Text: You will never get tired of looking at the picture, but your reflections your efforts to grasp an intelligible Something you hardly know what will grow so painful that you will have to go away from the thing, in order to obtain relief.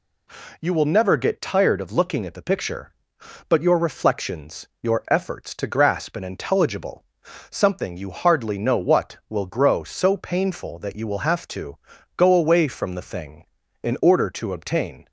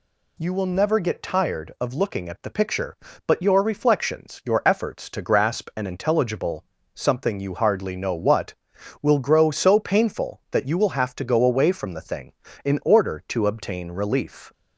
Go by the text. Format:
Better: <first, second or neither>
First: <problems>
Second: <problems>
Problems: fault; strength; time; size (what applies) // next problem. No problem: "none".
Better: second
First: pauses between "reflections" and "your"; slight; at 4.6 s; 0.16 s long // pauses between "intelligible" and "Something"; at 7.0 s; 0.44 s long // pauses between "to" and "go"; at 11.7 s; 0.40 s long // stops before "relief"; at 15.0 s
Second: pauses between "intelligible" and "Something"; slight; at 6.6 s; 0.30 s long